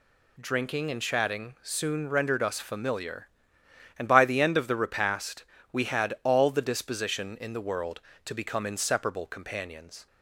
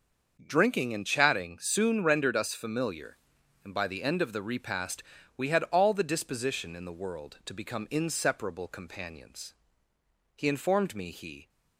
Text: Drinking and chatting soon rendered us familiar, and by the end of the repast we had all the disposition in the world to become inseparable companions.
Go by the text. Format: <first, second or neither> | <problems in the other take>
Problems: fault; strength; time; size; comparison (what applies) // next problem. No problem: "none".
first | starts louder than the rest; until 1.4 s; 6.5 dB // pauses between "repast" and "we"; slight; at 5.0 s; 0.34 s long; slight in the first // goes on to say "He informed me he"; noticeable; from 10.3 s on; 1.1 s long